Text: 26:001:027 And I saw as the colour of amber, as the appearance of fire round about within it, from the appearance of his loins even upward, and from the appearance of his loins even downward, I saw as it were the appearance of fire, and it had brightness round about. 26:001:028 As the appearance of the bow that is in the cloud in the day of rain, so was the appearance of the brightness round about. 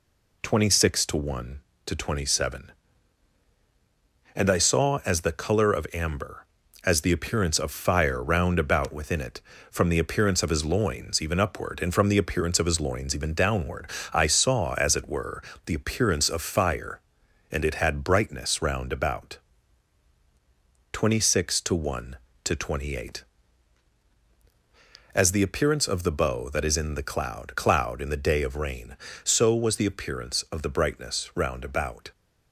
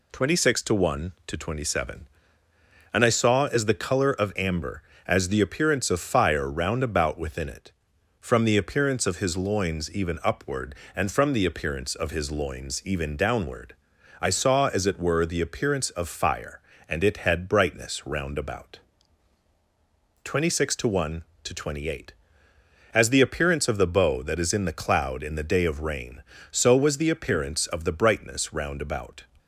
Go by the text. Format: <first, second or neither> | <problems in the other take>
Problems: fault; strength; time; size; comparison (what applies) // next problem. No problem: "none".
second | pauses between "were" and "the"; slight; at 15.4 s; 0.24 s long // says "cloud" twice; at 27.5 s